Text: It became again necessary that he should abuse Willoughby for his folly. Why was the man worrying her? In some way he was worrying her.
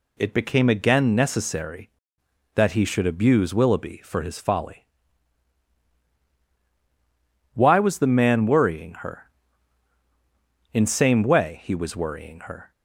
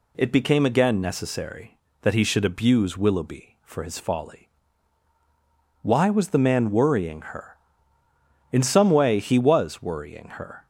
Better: second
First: says "same" for "some"; at 10.8 s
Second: none

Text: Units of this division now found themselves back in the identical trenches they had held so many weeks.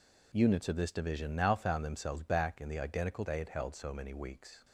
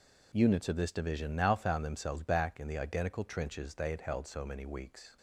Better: second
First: skips "trenches"; at 3.2 s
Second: none

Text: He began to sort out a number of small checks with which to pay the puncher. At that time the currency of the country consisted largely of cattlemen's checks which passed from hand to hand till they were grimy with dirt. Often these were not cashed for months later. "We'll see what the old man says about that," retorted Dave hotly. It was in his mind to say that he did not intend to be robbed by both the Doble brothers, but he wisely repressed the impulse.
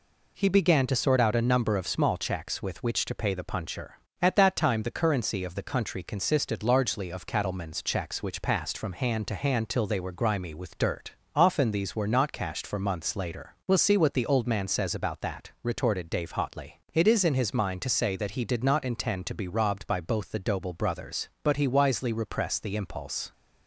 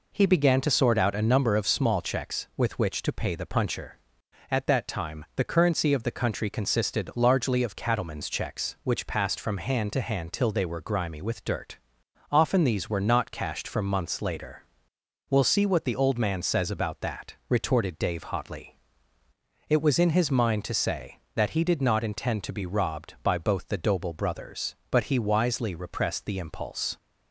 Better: second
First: says "is" for "was"; at 17.0 s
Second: none

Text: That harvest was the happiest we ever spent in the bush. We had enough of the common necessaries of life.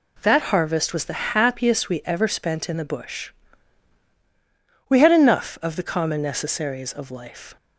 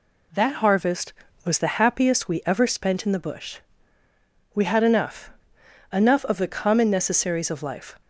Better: first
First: none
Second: says "enough" twice; at 5.9 s

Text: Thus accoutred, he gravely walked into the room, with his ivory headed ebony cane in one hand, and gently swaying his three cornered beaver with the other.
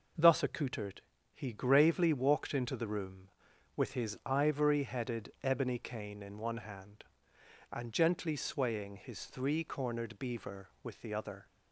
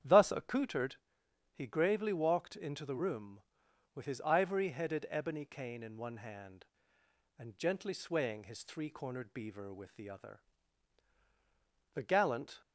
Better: first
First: none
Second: starts louder than the rest; strong; until 1.6 s; 9 dB // goes on to say "The gallant"; noticeable; from 11.9 s on; 0.68 s long

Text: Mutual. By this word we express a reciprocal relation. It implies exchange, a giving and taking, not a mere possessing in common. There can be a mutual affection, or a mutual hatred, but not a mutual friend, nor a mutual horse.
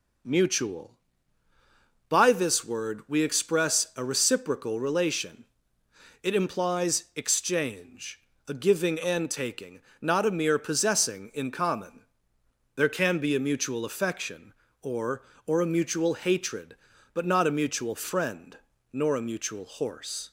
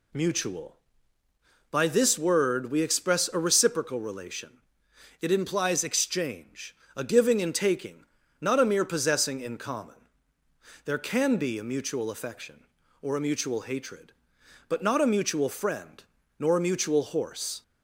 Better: second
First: says "or" twice; at 15.4 s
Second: none

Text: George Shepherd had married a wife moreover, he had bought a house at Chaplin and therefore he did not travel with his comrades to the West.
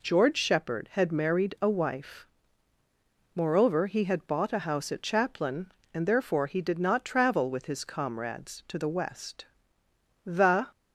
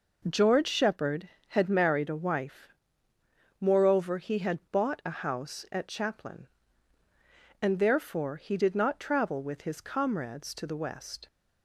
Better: second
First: pauses between "wife" and "moreover"; at 2.2 s; 1.0 s long // goes on to say "The"; slight; from 10.2 s on; 0.46 s long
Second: pauses between "wife" and "moreover"; noticeable; at 2.6 s; 0.90 s long

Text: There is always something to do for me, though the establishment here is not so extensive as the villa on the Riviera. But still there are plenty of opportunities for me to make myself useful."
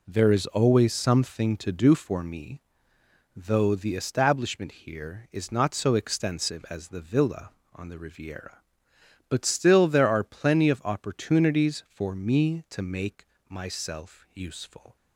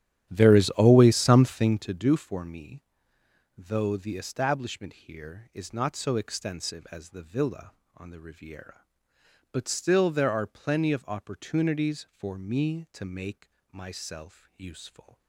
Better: first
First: pauses between "make" and "myself"; slight; at 13.2 s; 0.22 s long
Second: starts louder than the rest; strong; until 2.0 s; 11 dB // pauses between "make" and "myself"; slight; at 13.4 s; 0.22 s long

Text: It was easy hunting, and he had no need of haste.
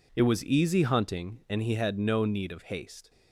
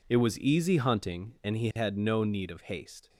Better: neither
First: none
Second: none

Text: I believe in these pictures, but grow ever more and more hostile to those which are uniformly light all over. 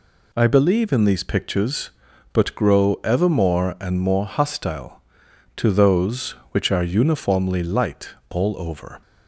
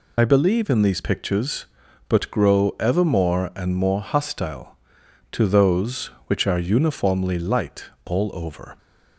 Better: first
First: pauses between "light" and "all"; slight; at 8.0 s; 0.22 s long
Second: loses the start of "I"; at 0.1 s; 65 ms // pauses between "light" and "all"; slight; at 7.8 s; 0.22 s long

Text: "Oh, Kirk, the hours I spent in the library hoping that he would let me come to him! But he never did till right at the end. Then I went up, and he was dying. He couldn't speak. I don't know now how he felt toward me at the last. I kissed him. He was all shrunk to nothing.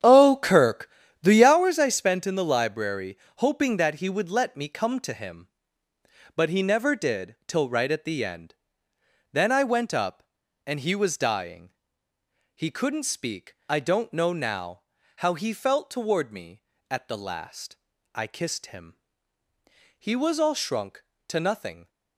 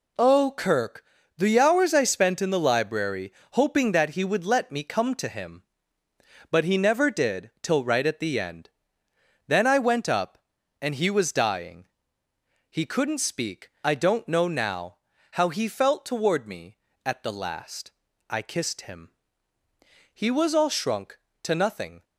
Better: second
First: starts louder than the rest; strong; until 1.6 s; 9 dB // pauses between "library" and "hoping"; slight; at 3.1 s; 0.20 s long // pauses between "now" and "how"; slight; at 14.8 s; 0.34 s long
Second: pauses between "library" and "hoping"; slight; at 3.3 s; 0.20 s long // pauses between "now" and "how"; slight; at 14.9 s; 0.34 s long

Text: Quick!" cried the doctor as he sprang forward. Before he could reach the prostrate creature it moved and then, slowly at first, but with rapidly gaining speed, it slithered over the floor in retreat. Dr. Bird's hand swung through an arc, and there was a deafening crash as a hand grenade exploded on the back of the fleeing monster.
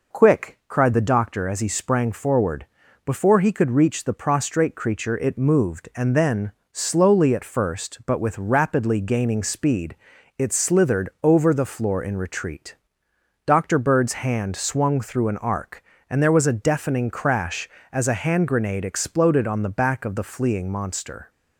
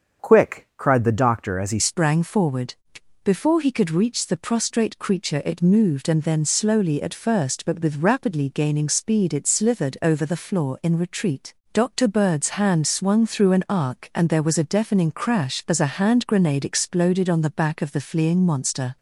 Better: first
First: none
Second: starts louder than the rest; until 1.2 s; 6.5 dB // changes voice at "sprang"; from 1.7 s on; 17.2 s long

